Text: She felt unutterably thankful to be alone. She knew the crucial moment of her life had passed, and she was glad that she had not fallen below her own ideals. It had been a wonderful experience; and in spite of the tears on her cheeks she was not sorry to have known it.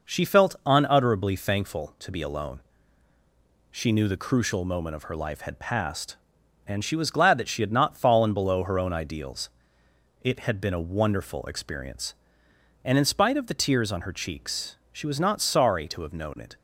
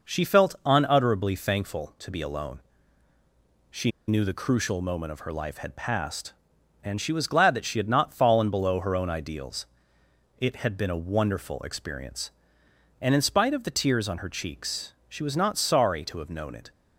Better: first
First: none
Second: pauses between "She" and "knew"; slight; at 3.9 s; 0.18 s long

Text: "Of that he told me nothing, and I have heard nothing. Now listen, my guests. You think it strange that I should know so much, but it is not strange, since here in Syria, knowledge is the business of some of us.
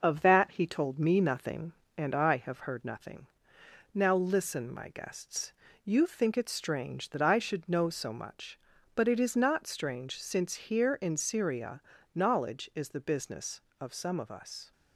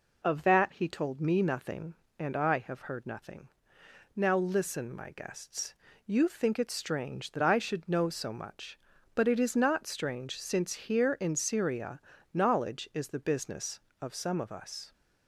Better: second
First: gets quieter; slight; throughout; 2.5 dB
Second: none

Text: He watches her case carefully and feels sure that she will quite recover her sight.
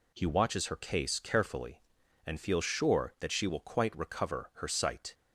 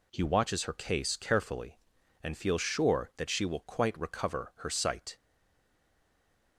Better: first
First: none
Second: stays silent after the last word; noticeable; from 5.1 s on; 1.4 s long

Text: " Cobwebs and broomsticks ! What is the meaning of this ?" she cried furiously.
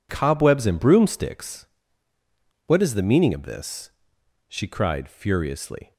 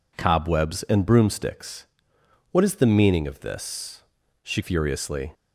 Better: first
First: none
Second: skips "cried"; at 4.6 s

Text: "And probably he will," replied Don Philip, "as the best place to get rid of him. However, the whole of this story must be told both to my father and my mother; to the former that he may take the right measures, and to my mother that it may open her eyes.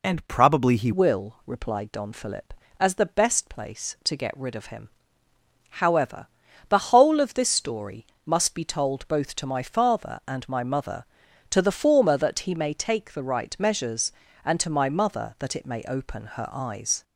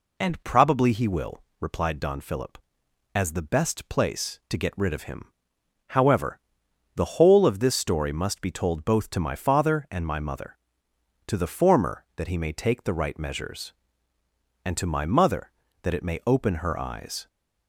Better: second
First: changes voice at "will"; from 0.9 s on; 16.1 s long // pauses between "story" and "must"; slight; at 8.0 s; 0.20 s long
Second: none

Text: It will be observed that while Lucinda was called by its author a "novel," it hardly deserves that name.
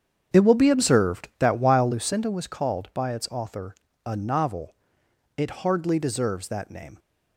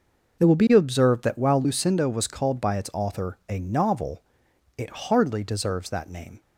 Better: second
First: starts louder than the rest; strong; until 2.2 s; 8 dB // pauses between "author" and "a"; slight; at 3.7 s; 0.30 s long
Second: none

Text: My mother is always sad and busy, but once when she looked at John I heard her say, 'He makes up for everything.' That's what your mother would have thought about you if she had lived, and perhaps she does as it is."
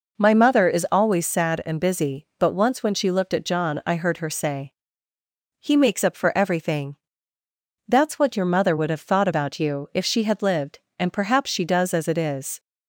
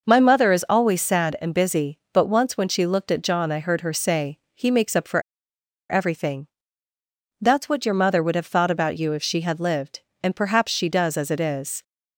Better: first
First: none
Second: pauses between "for" and "everything"; noticeable; at 5.2 s; 0.68 s long

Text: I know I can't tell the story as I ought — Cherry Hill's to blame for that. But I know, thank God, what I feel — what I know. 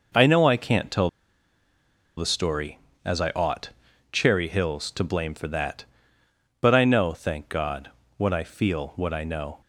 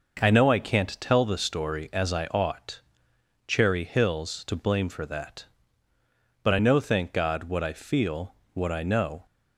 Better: second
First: pauses between "tell" and "the"; at 1.0 s; 1.0 s long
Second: none

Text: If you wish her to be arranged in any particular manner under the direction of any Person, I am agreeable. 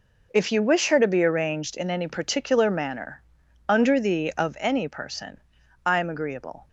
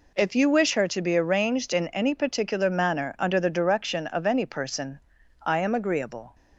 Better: second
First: pauses between "manner" and "under"; noticeable; at 3.1 s; 0.48 s long // skips "direction"; at 4.3 s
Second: none

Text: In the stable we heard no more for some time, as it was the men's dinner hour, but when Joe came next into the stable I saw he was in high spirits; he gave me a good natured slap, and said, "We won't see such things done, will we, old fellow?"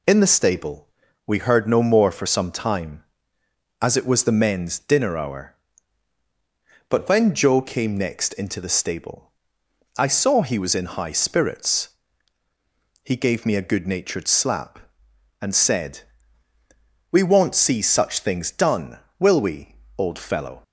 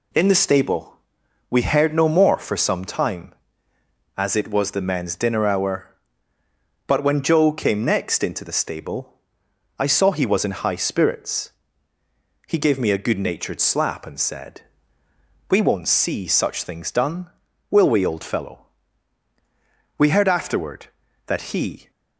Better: first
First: pauses between "stable" and "we"; at 0.8 s; 0.38 s long // pauses between "stable" and "I"; noticeable; at 9.3 s; 0.66 s long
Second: pauses between "stable" and "we"; noticeable; at 0.9 s; 0.52 s long // pauses between "stable" and "I"; noticeable; at 9.1 s; 0.60 s long // goes on to say "We heard afterward that he"; strong; from 19.9 s on; 1.9 s long

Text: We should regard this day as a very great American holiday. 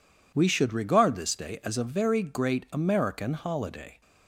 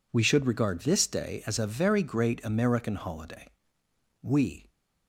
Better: first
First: none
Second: goes on to say "We"; slight; from 4.2 s on; 0.46 s long

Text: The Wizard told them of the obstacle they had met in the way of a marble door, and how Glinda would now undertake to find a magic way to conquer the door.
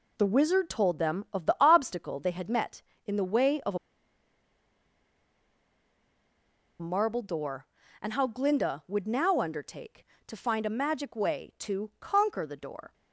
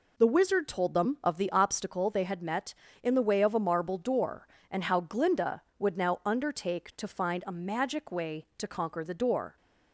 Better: second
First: pauses between "a" and "marble"; strong; at 3.7 s; 3.0 s long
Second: none

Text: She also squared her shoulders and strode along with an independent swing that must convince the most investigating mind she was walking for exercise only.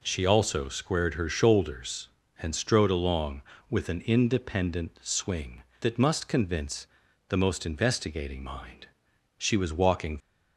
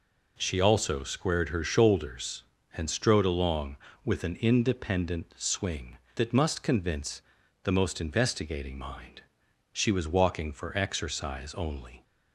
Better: second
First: pauses between "convince" and "the"; at 6.8 s; 0.40 s long // pauses between "mind" and "she"; noticeable; at 8.8 s; 0.50 s long // stops before "for exercise only"; at 10.2 s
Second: pauses between "convince" and "the"; at 7.2 s; 0.40 s long // pauses between "mind" and "she"; noticeable; at 9.2 s; 0.50 s long

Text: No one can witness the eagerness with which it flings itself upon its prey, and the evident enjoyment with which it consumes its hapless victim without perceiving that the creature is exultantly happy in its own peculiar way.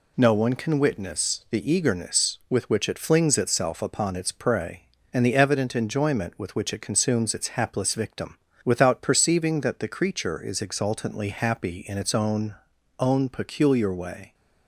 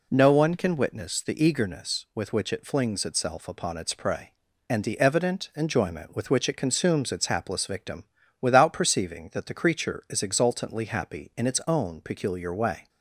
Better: second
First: pauses between "victim" and "without"; slight; at 8.3 s; 0.26 s long // says "own" twice; at 12.9 s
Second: pauses between "victim" and "without"; slight; at 8.0 s; 0.36 s long

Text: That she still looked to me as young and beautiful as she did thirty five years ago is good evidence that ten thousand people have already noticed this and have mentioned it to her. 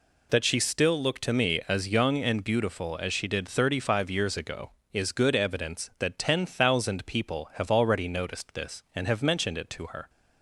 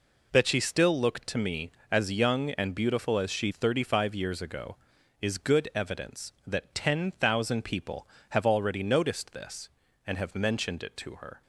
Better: first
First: none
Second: skips "did"; at 3.5 s

